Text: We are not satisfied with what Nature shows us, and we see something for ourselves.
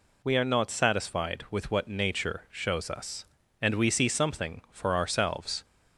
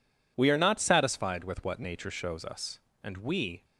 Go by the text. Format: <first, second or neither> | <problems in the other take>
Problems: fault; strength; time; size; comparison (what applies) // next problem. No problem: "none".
first | stops before "see something for ourselves"; at 3.6 s